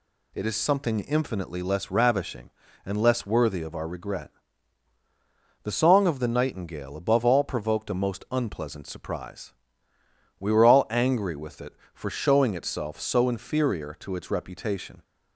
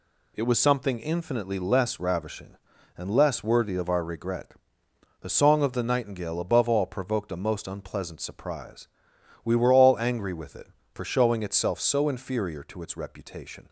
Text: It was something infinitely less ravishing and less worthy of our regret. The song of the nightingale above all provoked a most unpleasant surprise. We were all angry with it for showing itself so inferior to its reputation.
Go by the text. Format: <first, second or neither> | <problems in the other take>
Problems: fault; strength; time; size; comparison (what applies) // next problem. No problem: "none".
second | says "is" for "was"; at 0.4 s